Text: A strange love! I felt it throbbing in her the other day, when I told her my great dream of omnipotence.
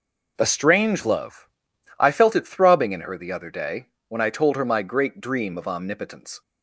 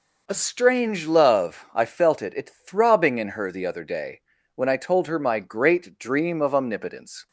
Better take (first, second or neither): first